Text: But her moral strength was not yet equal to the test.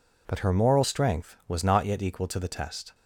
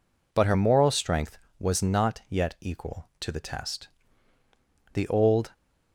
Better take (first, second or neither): first